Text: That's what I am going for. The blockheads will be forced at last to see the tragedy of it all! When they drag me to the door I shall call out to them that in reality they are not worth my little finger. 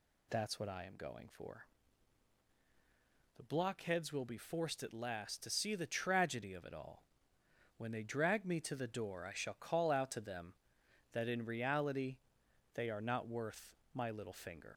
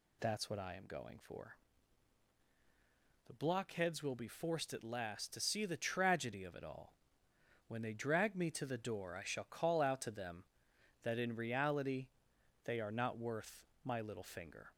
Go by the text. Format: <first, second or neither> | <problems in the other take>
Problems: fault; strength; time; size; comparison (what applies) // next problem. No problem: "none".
second | pauses between "reality" and "they"; noticeable; at 12.1 s; 0.58 s long; noticeable in the second // pauses between "worth" and "my"; slight; at 13.7 s; 0.18 s long; slight in the second // leaves "finger" unfinished; at 14.7 s; 65 ms